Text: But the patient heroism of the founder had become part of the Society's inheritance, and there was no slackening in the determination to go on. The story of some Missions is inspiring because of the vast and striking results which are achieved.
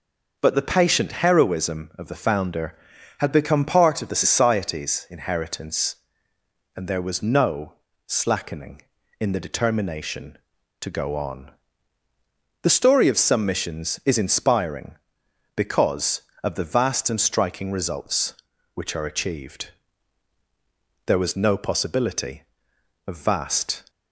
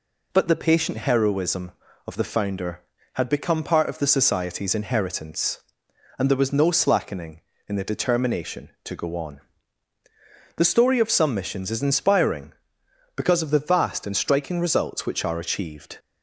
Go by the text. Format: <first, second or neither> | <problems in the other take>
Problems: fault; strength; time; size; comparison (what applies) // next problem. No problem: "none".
second | pauses between "no" and "slackening"; slight; at 7.7 s; 0.32 s long // goes on to say "There was no possibility of vast"; strong; from 21.0 s on; 2.8 s long